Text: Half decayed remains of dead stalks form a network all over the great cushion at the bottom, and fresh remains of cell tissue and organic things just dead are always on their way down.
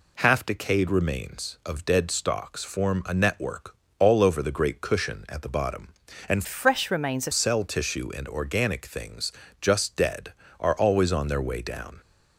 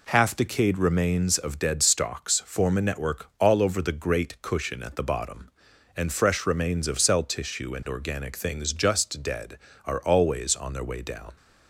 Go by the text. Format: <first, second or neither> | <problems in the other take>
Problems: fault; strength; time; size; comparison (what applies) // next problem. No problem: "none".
second | pauses between "network" and "all"; slight; at 3.7 s; 0.24 s long // changes voice from "fresh" to "of"; from 6.4 to 7.3 s; 0.9 s long // pauses between "things" and "just"; slight; at 9.3 s; 0.28 s long